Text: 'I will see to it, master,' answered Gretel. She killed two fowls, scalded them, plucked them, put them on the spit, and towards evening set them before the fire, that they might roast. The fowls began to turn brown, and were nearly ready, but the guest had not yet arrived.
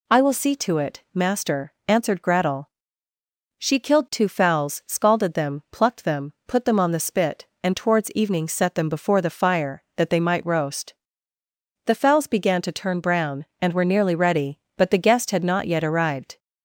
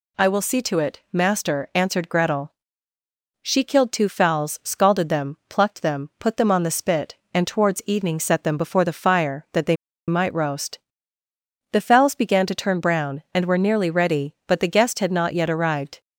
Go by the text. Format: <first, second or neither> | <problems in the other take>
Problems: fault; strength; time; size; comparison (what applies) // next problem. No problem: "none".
first | pauses between "they" and "might"; slight; at 9.7 s; 0.32 s long